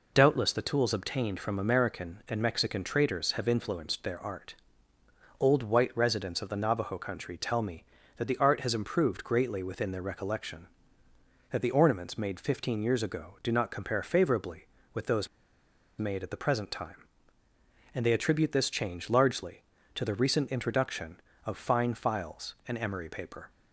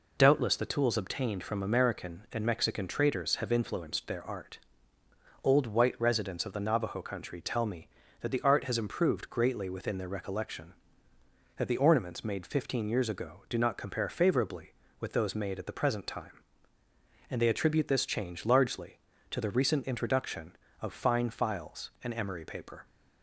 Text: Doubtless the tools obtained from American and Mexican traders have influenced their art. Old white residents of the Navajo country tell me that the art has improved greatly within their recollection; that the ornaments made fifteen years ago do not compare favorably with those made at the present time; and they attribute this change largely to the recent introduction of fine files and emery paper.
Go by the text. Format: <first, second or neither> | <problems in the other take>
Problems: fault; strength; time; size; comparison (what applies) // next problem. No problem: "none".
second | pauses between "those" and "made"; noticeable; at 15.2 s; 0.71 s long